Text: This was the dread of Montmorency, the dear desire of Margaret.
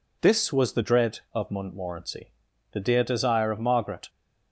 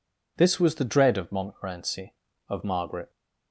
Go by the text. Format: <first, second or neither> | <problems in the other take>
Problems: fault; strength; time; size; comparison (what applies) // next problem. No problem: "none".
first | skips "the dear desire"; at 2.3 s